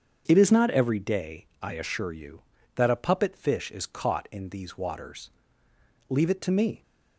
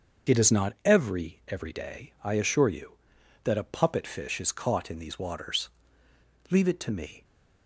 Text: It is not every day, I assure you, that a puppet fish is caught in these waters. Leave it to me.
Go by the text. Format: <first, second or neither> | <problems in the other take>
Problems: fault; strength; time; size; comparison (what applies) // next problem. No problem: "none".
first | starts louder than the rest; until 1.3 s; 6.5 dB; also in the first // says "every" twice; at 1.4 s